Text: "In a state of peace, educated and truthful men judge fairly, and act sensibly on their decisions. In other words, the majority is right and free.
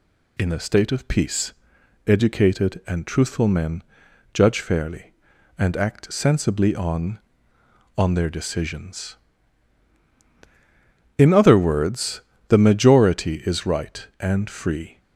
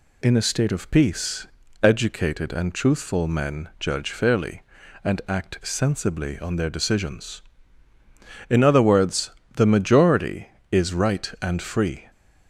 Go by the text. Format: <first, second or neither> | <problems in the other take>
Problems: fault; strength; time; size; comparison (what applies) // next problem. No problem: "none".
second | pauses between "men" and "judge"; noticeable; at 3.8 s; 0.52 s long // says "on" twice; at 7.9 s